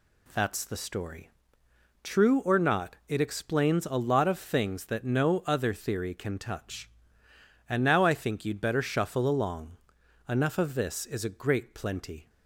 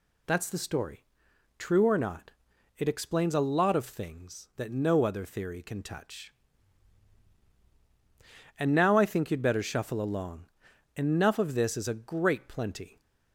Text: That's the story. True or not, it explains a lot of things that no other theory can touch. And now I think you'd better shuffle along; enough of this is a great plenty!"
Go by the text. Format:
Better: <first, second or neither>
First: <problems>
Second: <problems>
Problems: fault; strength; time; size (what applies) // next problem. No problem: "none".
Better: neither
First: none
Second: none